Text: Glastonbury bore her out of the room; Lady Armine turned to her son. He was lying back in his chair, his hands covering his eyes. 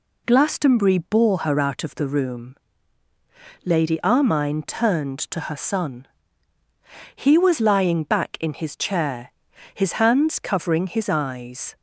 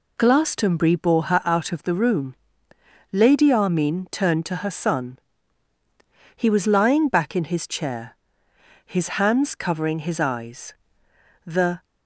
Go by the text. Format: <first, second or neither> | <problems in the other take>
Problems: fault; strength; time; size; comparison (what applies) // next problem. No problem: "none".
first | goes on to say "The"; slight; from 11.4 s on; 0.36 s long